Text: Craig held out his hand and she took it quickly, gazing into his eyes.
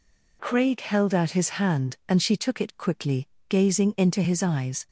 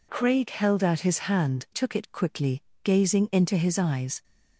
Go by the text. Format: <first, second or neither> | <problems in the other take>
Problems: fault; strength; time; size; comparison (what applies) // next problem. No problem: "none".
first | skips "and she"; at 1.6 s